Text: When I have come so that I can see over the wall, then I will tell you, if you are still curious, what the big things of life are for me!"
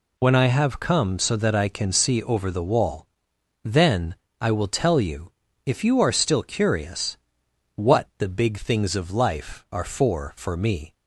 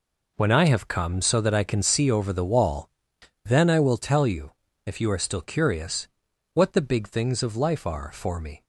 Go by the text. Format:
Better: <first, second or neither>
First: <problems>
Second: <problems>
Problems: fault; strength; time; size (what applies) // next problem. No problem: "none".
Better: second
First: pauses between "then" and "I"; slight; at 4.1 s; 0.26 s long // says "for" twice; at 10.3 s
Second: none